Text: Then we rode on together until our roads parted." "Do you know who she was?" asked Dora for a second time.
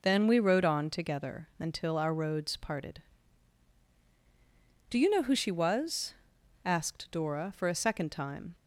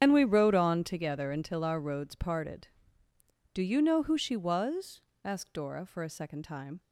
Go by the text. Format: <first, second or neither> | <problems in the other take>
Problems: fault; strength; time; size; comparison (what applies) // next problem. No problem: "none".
first | loses the start of "Then"; at 0.0 s; 105 ms // starts louder than the rest; strong; until 1.0 s; 8 dB